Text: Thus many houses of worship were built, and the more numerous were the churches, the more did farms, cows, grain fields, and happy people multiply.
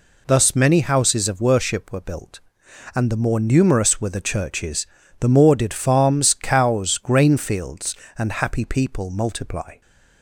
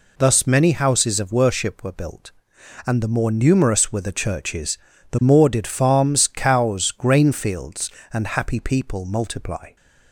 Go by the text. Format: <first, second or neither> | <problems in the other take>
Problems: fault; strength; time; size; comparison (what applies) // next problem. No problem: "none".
neither | none